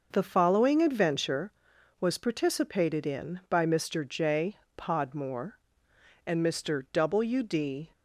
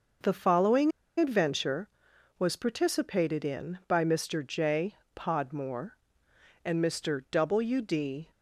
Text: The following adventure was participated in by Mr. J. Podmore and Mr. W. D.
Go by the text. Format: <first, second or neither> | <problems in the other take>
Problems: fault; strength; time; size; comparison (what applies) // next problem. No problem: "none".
first | pauses between "following" and "adventure"; slight; at 0.9 s; 0.27 s long